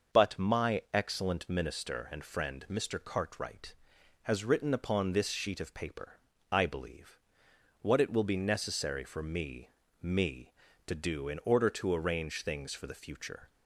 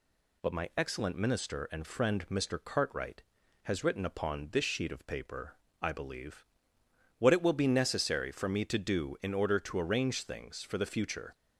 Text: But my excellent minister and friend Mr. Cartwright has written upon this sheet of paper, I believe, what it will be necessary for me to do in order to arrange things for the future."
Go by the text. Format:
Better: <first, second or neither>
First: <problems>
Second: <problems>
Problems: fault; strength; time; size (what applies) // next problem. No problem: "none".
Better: second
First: starts louder than the rest; until 1.2 s; 6 dB // says "me" twice; at 10.0 s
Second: none